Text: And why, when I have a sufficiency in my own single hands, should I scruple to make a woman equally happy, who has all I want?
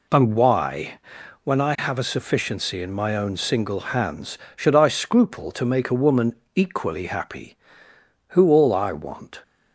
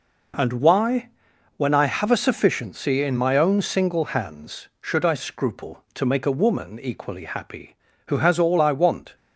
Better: second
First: pauses between "woman" and "equally"; slight; at 6.3 s; 0.22 s long // skips "has"; at 8.5 s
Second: none

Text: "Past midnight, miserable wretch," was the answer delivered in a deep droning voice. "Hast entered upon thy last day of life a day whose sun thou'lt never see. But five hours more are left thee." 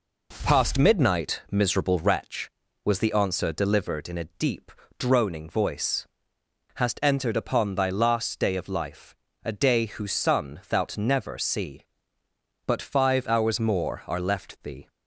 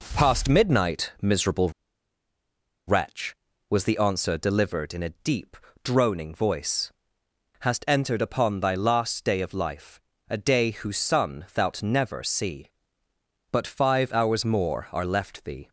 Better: first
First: pauses between "deep" and "droning"; slight; at 4.7 s; 0.26 s long // pauses between "life" and "a"; slight; at 9.1 s; 0.30 s long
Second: pauses between "miserable" and "wretch"; at 1.6 s; 1.1 s long // pauses between "deep" and "droning"; slight; at 5.5 s; 0.26 s long // pauses between "life" and "a"; slight; at 9.9 s; 0.30 s long

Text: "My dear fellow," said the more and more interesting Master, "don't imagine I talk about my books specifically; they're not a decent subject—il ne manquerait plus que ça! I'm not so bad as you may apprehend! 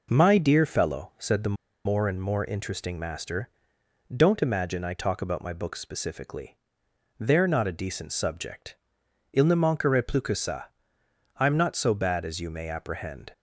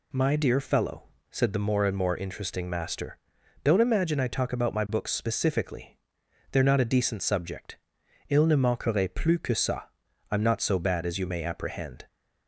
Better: second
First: pauses between "the" and "more"; slight; at 1.5 s; 0.31 s long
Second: none

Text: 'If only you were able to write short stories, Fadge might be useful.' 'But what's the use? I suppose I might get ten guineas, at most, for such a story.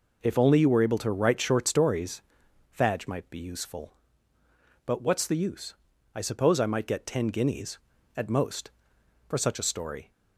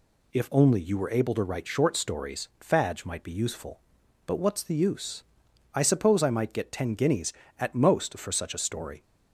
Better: neither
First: none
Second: none

